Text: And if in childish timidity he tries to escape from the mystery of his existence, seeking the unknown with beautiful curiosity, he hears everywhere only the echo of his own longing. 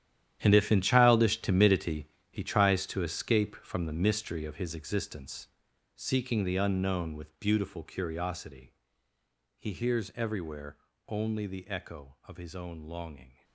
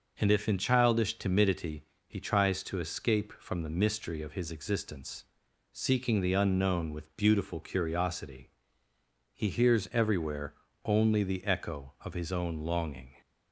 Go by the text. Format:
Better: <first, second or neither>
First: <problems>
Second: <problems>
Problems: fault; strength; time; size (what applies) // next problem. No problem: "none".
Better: second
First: gets quieter; strong; throughout; 14.5 dB // pauses between "timidity" and "he"; slight; at 2.0 s; 0.24 s long // pauses between "everywhere" and "only"; slight; at 10.7 s; 0.32 s long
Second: pauses between "timidity" and "he"; slight; at 1.8 s; 0.24 s long // pauses between "everywhere" and "only"; slight; at 10.5 s; 0.32 s long